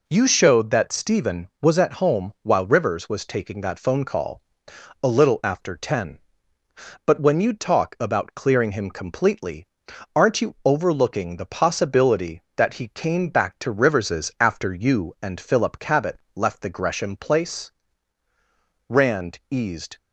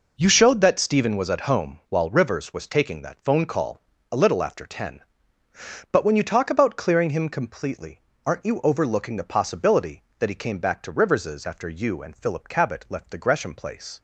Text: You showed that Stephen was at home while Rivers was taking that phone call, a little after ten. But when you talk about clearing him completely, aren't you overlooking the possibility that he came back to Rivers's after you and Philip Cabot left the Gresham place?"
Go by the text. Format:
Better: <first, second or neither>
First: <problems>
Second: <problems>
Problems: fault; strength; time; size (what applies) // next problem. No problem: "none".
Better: second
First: pauses between "Cabot" and "left"; slight; at 16.1 s; 0.16 s long // goes on to say "Rand eased"; noticeable; from 18.8 s on; 1.1 s long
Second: none